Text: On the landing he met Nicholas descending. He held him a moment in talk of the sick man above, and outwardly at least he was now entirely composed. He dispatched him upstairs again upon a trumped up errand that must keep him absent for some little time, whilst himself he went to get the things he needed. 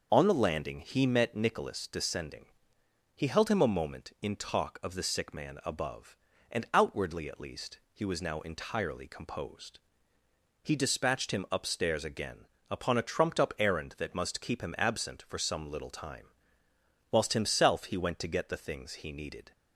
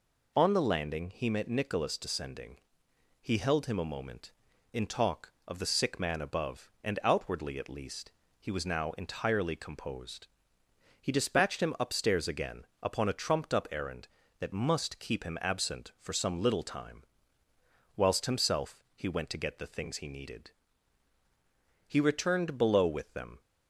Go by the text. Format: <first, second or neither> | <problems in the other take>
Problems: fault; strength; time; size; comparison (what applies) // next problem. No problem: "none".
first | pauses between "least" and "he"; slight; at 8.1 s; 0.26 s long; slight in the first // pauses between "again" and "upon"; slight; at 12.6 s; 0.16 s long; slight in the first // goes on to say "He returned below with them"; from 21.8 s on; 1.5 s long